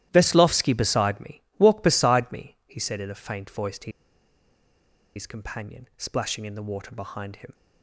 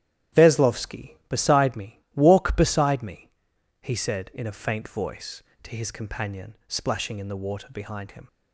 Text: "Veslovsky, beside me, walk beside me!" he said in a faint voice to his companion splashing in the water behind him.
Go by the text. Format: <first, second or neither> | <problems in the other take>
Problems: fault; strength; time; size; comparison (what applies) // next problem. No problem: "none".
second | starts louder than the rest; strong; until 1.1 s; 13.5 dB; strong in the second // pauses between "to" and "his"; strong; at 3.9 s; 1.2 s long